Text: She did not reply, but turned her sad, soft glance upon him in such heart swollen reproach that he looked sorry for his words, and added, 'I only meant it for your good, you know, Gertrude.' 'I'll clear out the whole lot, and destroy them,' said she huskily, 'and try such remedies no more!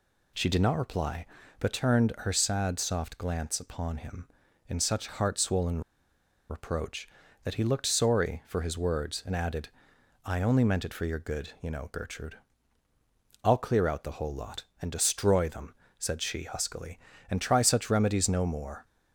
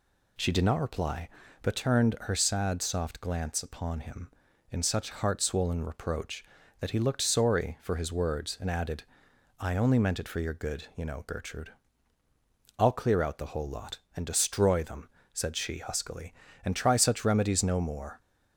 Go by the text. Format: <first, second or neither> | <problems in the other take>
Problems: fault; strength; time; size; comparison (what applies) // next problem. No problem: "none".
second | pauses between "swollen" and "reproach"; noticeable; at 5.8 s; 0.69 s long